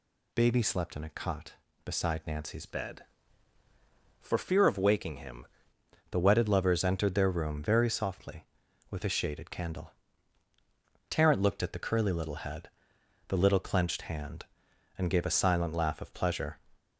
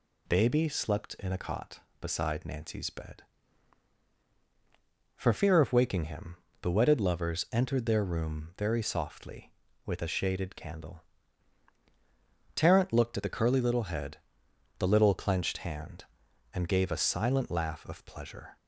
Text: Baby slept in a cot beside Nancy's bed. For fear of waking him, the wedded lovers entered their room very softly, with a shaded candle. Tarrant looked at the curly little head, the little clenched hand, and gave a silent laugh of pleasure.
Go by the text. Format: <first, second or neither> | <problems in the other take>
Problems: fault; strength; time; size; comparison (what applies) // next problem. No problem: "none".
second | changes voice from "bed" to "him"; from 2.6 to 5.4 s; 2.8 s long